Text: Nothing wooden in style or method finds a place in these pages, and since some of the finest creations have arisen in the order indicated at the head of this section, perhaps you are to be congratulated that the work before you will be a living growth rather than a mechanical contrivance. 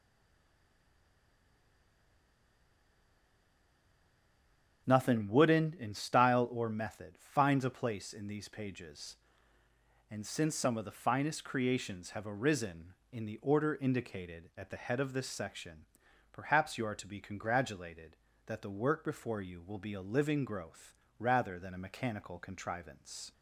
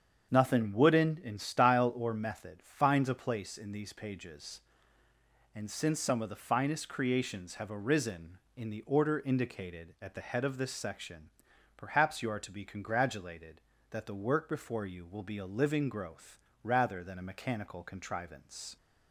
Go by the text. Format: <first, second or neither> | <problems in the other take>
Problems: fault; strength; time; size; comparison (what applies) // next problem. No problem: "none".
second | stays silent before the first word; strong; until 4.8 s; 4.8 s long // starts louder than the rest; strong; until 5.8 s; 7.5 dB; strong in the second // pauses between "growth" and "rather"; slight; at 20.9 s; 0.20 s long; slight in the second